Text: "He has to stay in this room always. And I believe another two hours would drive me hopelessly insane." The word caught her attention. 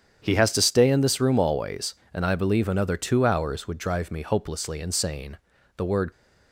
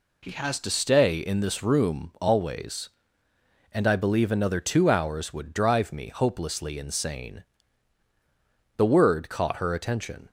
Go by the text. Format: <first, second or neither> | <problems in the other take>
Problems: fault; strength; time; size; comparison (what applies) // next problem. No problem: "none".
second | starts louder than the rest; strong; until 1.2 s; 8.5 dB // stops before "caught her attention"; at 6.1 s